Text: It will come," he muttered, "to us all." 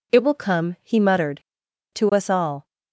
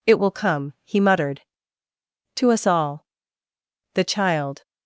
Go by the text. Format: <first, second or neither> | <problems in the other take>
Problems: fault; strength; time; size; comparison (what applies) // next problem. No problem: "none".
first | goes on to say "The child"; noticeable; from 3.9 s on; 0.70 s long